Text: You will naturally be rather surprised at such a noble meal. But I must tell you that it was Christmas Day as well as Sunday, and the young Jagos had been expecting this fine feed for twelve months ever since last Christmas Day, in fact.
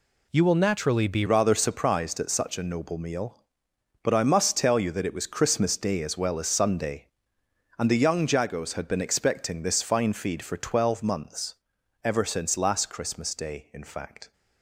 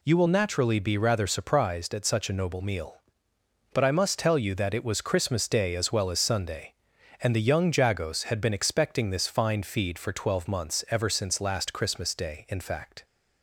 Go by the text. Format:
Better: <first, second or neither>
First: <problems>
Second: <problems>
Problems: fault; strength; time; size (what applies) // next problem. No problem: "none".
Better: second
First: changes voice at "rather"; from 1.2 s on; 13.1 s long // pauses between "months" and "ever"; noticeable; at 11.5 s; 0.46 s long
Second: none